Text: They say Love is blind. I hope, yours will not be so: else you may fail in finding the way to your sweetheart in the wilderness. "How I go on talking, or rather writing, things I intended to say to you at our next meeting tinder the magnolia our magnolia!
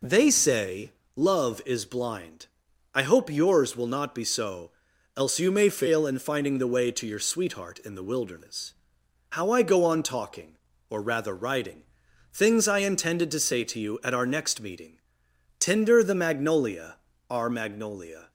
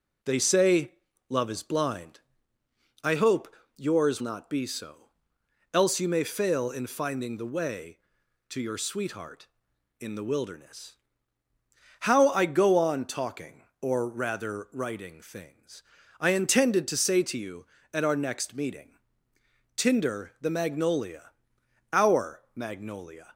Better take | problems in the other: first | pauses between "say" and "Love"; at 0.9 s; 0.38 s long; slight in the first // skips "will"; at 4.2 s // pauses between "things" and "I"; at 15.8 s; 0.38 s long // pauses between "meeting" and "tinder"; noticeable; at 18.9 s; 0.76 s long; noticeable in the first // pauses between "magnolia" and "our"; noticeable; at 21.3 s; 0.60 s long; slight in the first

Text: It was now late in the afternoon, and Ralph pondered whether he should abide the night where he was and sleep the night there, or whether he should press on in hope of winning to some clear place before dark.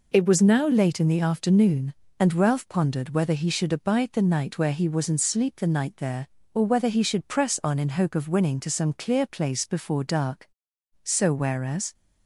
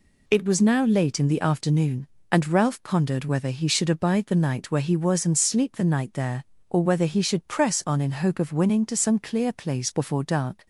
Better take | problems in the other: second | goes on to say "So whereas"; noticeable; from 11.0 s on; 0.88 s long

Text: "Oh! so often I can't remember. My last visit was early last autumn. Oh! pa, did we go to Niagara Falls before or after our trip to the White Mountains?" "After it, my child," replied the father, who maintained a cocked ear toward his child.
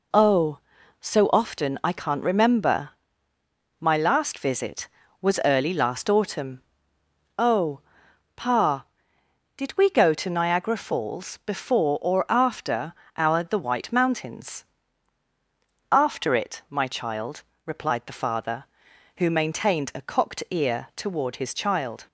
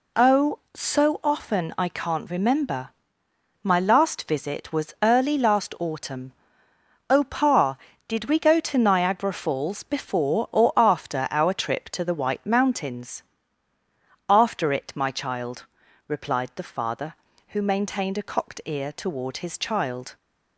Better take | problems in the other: second | pauses between "after" and "our"; slight; at 12.9 s; 0.24 s long // skips "trip to"; at 13.4 s

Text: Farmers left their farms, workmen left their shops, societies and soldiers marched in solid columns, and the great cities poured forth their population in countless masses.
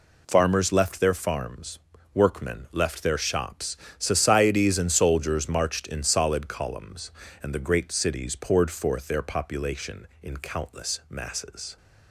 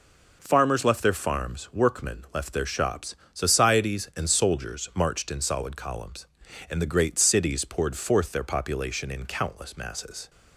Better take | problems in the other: neither | none

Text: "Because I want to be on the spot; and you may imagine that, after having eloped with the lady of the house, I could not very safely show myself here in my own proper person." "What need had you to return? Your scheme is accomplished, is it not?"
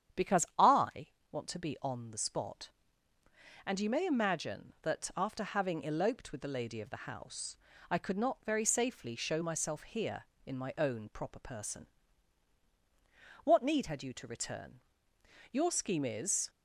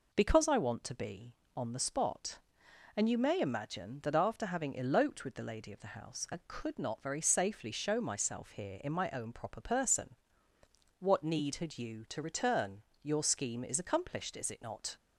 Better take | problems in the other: second | starts louder than the rest; strong; until 1.5 s; 9 dB // pauses between "I" and "want"; slight; at 1.0 s; 0.24 s long // stops before "accomplished is it not"; at 16.4 s

